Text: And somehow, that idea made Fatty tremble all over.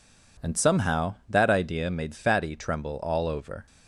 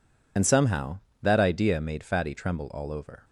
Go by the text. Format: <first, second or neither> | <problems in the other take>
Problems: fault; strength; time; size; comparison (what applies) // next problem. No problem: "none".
first | loses the start of "And"; at 0.3 s; 50 ms